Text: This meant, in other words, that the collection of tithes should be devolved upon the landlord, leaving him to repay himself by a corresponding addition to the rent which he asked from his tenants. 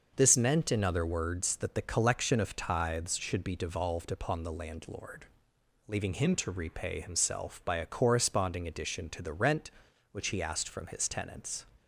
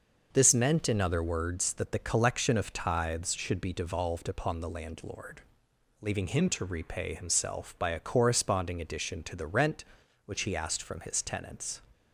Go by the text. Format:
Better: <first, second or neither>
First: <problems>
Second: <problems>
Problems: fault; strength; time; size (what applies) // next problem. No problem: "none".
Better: neither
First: none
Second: none